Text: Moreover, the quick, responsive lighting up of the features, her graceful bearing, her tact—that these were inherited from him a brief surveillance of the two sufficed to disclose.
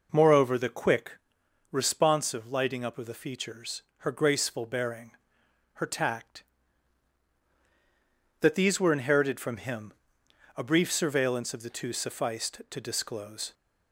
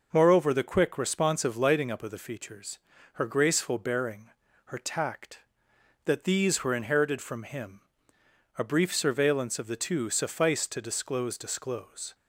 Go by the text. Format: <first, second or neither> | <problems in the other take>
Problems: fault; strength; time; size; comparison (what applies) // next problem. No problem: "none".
first | pauses between "him" and "a"; noticeable; at 7.8 s; 0.74 s long; noticeable in the first // says "disclose" twice; at 11.3 s